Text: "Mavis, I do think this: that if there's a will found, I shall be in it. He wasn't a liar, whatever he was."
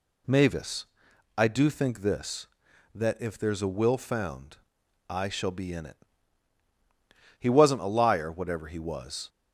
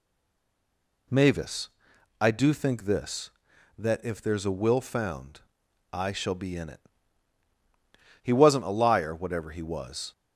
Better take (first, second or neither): first